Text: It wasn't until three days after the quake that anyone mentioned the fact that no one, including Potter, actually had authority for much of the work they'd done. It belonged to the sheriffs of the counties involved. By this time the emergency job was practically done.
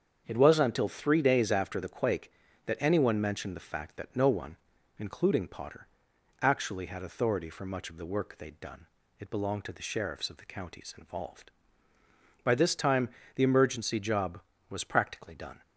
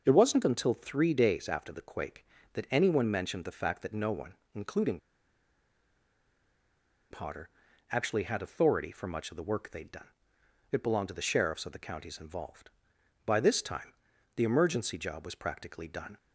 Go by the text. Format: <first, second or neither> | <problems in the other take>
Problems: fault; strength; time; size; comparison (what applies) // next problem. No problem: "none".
first | starts louder than the rest; until 1.0 s; 6 dB; strong in the first // pauses between "including" and "Potter"; strong; at 4.9 s; 2.1 s long // pauses between "time" and "the"; at 13.9 s; 0.42 s long; slight in the first